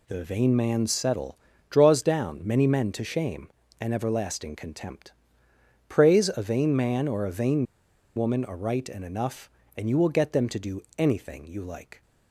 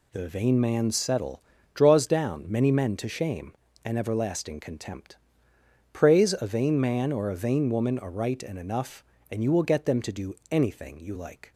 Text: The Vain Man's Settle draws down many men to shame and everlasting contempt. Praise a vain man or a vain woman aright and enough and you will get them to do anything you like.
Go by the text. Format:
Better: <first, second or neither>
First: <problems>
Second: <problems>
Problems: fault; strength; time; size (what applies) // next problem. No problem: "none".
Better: second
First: pauses between "Settle" and "draws"; slight; at 1.3 s; 0.36 s long // pauses between "vain" and "woman"; noticeable; at 7.6 s; 0.50 s long // pauses between "do" and "anything"; slight; at 10.8 s; 0.16 s long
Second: pauses between "Settle" and "draws"; slight; at 1.3 s; 0.36 s long // pauses between "do" and "anything"; slight; at 10.3 s; 0.16 s long